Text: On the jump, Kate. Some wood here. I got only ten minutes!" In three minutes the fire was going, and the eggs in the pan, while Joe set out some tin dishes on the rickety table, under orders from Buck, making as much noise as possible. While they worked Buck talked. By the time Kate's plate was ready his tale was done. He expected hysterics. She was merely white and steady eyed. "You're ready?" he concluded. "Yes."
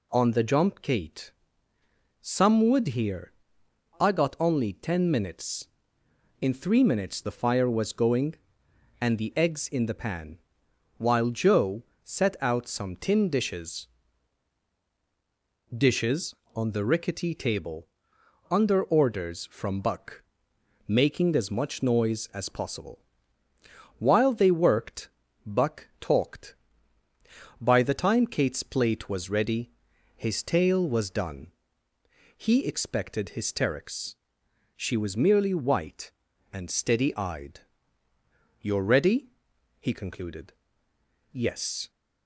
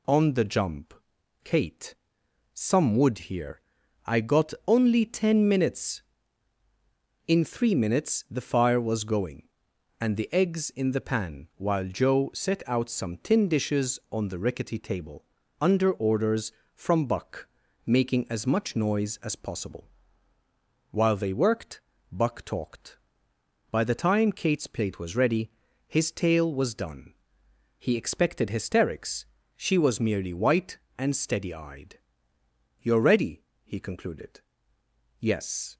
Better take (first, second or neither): second